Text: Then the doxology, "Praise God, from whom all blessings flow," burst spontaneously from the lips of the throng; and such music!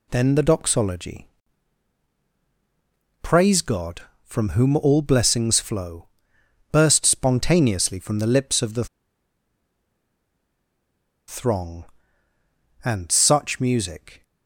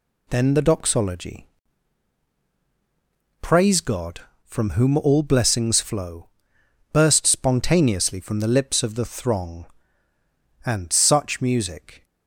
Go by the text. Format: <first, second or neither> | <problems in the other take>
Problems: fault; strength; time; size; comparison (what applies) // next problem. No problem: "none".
second | pauses between "the" and "throng"; strong; at 8.8 s; 2.4 s long